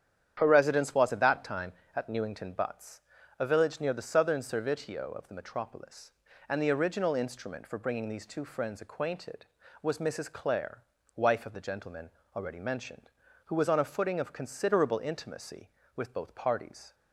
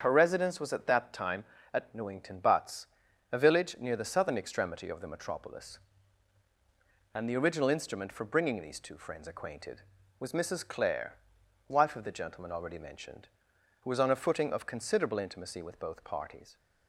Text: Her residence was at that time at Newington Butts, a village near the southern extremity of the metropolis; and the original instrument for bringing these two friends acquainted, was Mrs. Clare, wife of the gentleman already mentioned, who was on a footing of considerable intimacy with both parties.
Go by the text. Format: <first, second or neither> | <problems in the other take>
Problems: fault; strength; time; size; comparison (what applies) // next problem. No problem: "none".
second | starts louder than the rest; strong; until 1.3 s; 9.5 dB; strong in the second // says "servitio" for "extremity"; at 4.4 s // pauses between "gentleman" and "already"; slight; at 12.1 s; 0.26 s long